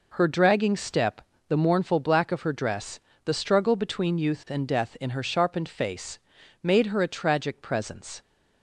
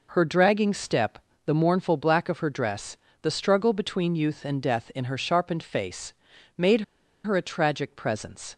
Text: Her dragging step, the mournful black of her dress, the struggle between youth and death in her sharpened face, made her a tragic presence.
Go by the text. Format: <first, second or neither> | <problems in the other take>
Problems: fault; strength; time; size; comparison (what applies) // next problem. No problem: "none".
first | pauses between "made" and "her"; at 6.7 s; 0.44 s long